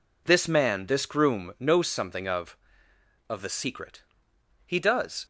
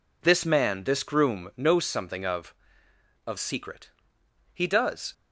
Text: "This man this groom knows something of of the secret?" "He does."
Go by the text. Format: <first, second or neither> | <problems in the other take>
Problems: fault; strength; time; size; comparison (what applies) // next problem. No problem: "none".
first | skips "the"; at 3.3 s